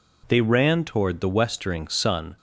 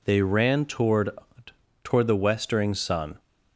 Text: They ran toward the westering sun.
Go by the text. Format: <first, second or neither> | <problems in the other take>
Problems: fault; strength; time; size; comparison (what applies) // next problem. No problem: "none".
first | says "toward" twice; at 1.8 s